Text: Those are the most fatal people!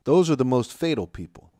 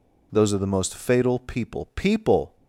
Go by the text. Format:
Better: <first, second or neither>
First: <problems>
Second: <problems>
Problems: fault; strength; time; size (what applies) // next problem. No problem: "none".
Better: first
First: none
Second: says "people" twice; at 1.9 s